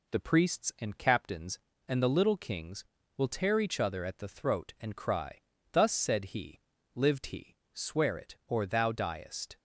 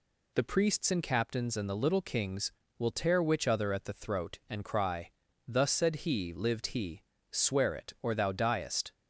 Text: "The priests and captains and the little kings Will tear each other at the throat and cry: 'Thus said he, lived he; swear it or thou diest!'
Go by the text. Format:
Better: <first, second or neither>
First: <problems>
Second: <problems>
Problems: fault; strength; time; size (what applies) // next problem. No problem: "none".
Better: first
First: none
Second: says "which" for "each"; at 3.2 s